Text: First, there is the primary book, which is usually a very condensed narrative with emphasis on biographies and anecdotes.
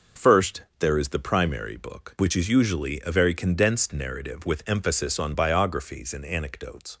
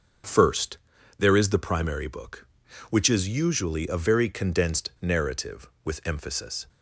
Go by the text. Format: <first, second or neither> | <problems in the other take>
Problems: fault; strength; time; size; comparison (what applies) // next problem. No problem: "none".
first | stops before "on biographies and anecdotes"; at 6.6 s